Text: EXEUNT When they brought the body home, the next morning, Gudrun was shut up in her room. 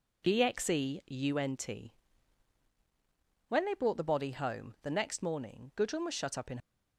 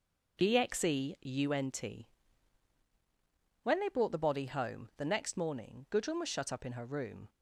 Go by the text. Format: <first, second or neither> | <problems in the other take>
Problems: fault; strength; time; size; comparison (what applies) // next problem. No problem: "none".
second | pauses between "EXEUNT" and "When"; strong; at 1.9 s; 1.5 s long; strong in the second // stops before "her room"; at 6.5 s